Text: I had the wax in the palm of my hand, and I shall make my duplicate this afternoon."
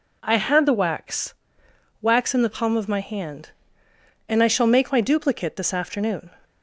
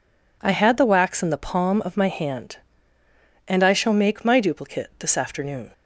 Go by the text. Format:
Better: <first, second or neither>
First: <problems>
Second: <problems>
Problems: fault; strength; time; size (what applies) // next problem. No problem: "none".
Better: second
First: says "wax" twice; at 2.0 s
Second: none